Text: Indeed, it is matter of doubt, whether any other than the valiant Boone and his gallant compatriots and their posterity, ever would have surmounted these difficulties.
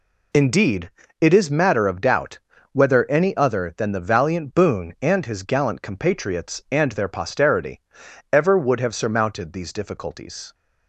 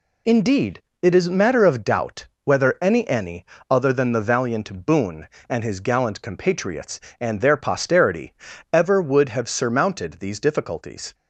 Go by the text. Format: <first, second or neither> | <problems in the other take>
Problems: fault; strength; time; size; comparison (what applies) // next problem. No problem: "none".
first | says "any" twice; at 3.0 s